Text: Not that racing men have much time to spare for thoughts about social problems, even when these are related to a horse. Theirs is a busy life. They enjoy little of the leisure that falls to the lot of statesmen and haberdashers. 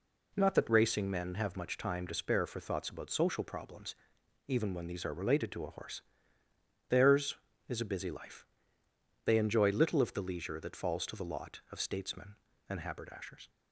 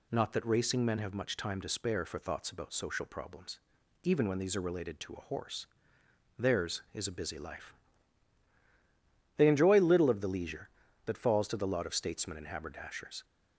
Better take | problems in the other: neither | none

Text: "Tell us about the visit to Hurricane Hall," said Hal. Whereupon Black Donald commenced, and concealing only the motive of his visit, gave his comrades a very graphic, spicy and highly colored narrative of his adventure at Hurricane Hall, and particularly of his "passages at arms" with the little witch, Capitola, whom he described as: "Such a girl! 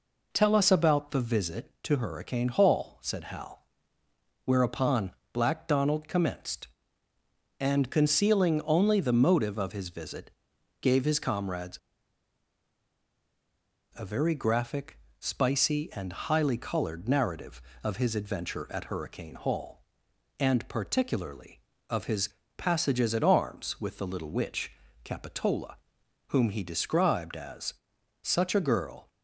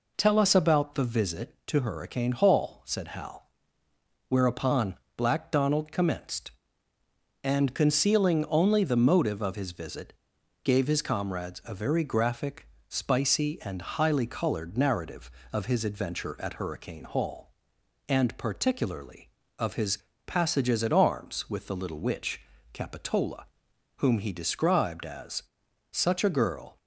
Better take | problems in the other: second | pauses between "Whereupon" and "Black"; slight; at 5.1 s; 0.22 s long; slight in the second // pauses between "comrades" and "a"; strong; at 11.7 s; 2.1 s long // pauses between "his" and "passages"; slight; at 22.2 s; 0.28 s long; slight in the second

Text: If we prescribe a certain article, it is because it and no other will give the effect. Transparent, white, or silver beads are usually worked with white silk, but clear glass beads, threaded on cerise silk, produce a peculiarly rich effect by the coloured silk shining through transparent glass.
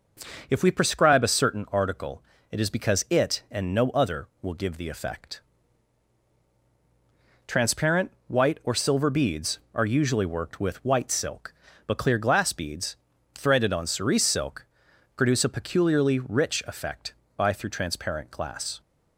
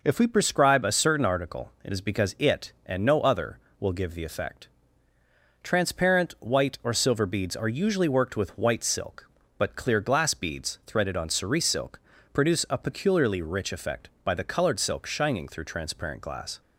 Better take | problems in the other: second | starts louder than the rest; until 1.5 s; 6 dB // skips "the coloured silk shining"; at 17.5 s

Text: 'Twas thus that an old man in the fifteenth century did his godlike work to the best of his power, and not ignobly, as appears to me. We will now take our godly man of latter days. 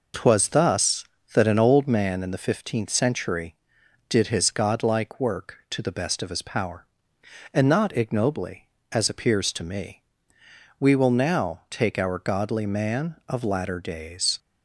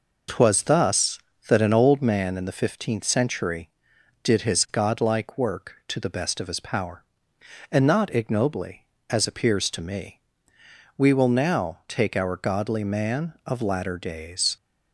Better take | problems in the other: neither | none

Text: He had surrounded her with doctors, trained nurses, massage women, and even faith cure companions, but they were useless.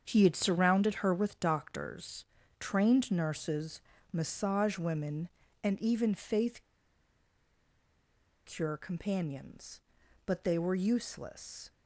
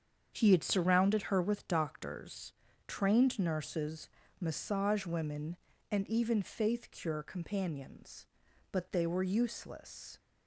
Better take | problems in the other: second | starts louder than the rest; strong; until 1.0 s; 7.5 dB; strong in the second // pauses between "faith" and "cure"; strong; at 6.6 s; 1.8 s long

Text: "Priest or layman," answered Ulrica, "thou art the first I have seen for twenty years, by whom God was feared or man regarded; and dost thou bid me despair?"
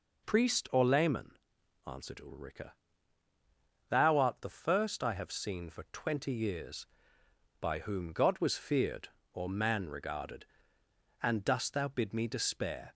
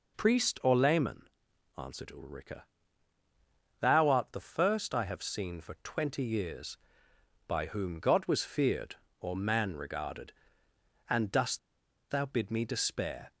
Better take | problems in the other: first | pauses between "dost" and "thou"; noticeable; at 11.5 s; 0.51 s long

